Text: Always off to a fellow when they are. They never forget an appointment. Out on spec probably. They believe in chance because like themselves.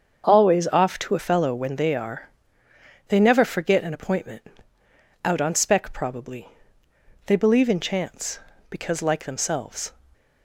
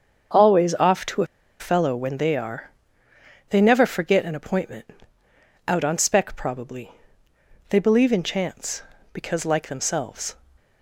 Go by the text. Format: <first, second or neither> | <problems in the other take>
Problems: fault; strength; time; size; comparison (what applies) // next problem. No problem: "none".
first | starts louder than the rest; until 1.7 s; 7 dB; also in the first // pauses between "a" and "fellow"; slight; at 1.2 s; 0.34 s long